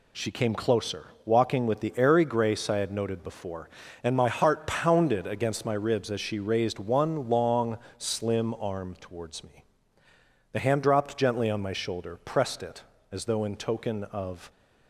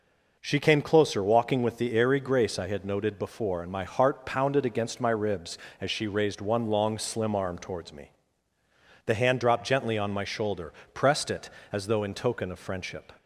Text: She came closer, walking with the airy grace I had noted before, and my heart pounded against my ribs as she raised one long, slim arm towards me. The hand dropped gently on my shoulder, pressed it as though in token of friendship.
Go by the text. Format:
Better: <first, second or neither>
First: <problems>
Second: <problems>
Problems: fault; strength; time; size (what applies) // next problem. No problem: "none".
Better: second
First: stops before "friendship"; at 14.4 s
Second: none